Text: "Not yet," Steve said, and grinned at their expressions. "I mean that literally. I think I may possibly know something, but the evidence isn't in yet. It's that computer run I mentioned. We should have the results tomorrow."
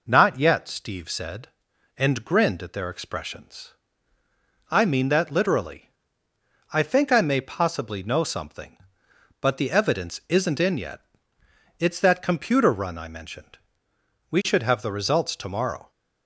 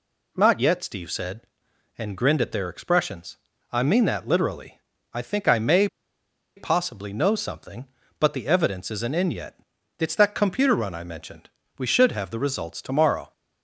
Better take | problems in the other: first | pauses between "may" and "possibly"; noticeable; at 5.8 s; 0.69 s long

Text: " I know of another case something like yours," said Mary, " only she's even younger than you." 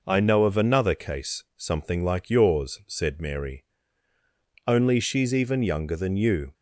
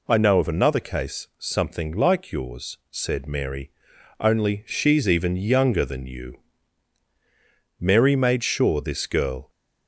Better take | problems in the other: first | goes on to say "Mary made sure this girl"; strong; from 7.7 s on; 1.7 s long

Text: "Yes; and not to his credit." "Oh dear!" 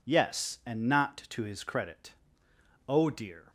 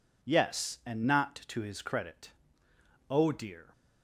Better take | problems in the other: neither | none

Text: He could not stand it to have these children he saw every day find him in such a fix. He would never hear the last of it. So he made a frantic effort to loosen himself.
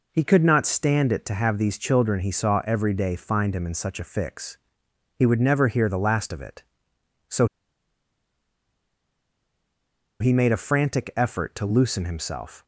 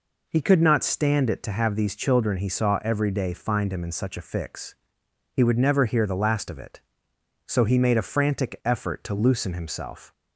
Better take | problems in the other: second | pauses between "So" and "he"; strong; at 7.4 s; 2.7 s long

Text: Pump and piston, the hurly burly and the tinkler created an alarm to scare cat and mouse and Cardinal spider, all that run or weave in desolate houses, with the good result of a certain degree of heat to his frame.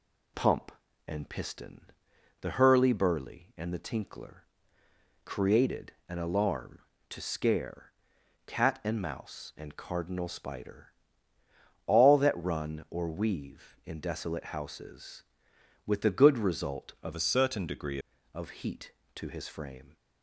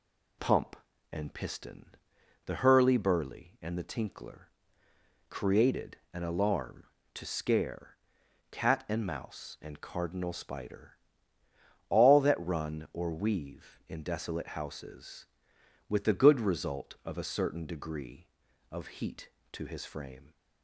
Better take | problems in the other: second | pauses between "tinkler" and "created"; noticeable; at 4.4 s; 0.80 s long; noticeable in the second // pauses between "created" and "an"; slight; at 5.9 s; 0.16 s long; slight in the second // pauses between "scare" and "cat"; noticeable; at 7.9 s; 0.52 s long; noticeable in the second // changes voice from "a" to "degree"; from 17.1 to 17.9 s; 0.8 s long

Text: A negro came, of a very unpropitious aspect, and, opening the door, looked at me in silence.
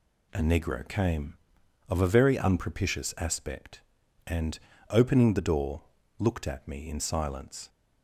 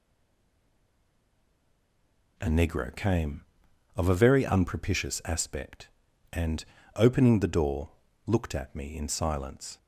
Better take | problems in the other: first | stays silent before the first word; until 2.3 s; 2.3 s long

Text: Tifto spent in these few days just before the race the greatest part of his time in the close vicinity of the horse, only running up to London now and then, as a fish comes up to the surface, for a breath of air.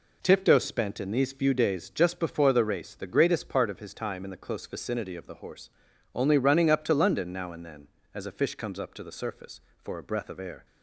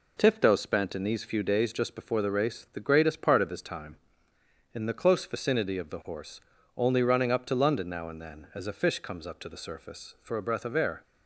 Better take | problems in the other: neither | none

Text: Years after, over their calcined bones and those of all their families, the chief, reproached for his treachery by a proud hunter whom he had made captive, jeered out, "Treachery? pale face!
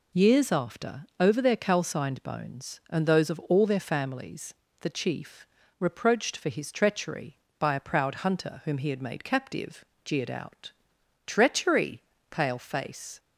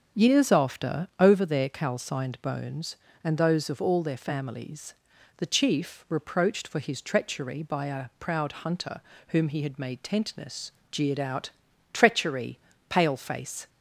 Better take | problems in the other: first | starts louder than the rest; until 1.2 s; 7 dB // pauses between "hunter" and "whom"; slight; at 9.0 s; 0.28 s long // says "tentness" for "captive"; at 10.0 s

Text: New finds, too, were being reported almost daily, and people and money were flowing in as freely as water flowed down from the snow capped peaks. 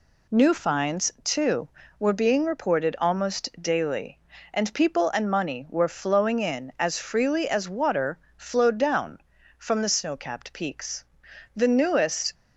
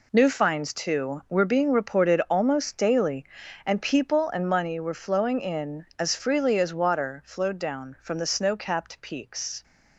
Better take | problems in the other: second | pauses between "water" and "flowed"; slight; at 8.1 s; 0.18 s long // goes on to say "The newest"; noticeable; from 11.5 s on; 0.78 s long

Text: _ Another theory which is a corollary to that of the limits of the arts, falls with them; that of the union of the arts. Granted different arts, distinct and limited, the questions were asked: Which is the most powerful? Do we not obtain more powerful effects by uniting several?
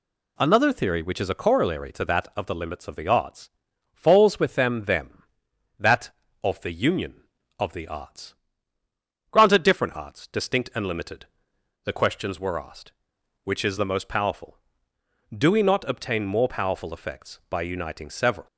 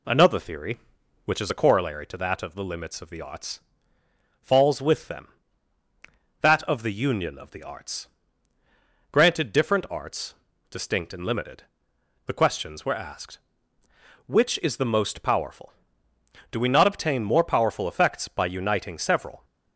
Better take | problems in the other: second | says "them" twice; at 4.8 s

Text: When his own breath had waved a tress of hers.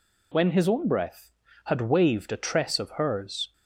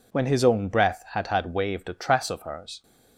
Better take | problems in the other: first | says "had" twice; at 1.2 s

